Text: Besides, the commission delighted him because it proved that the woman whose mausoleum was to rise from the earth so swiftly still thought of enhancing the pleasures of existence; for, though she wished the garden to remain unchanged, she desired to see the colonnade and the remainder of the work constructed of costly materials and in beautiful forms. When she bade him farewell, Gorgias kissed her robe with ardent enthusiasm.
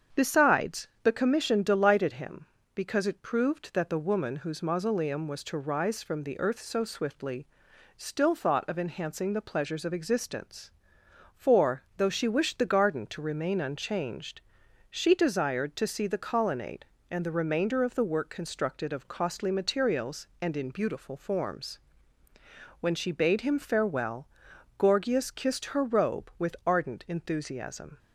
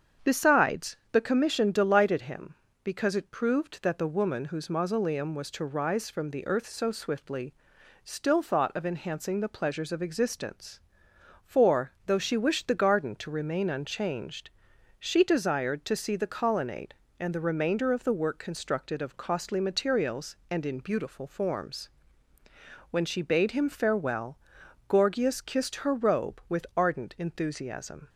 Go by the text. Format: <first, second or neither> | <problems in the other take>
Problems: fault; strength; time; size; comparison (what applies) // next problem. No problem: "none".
neither | starts louder than the rest; strong; the same in both // pauses between "swiftly" and "still"; noticeable; the same in both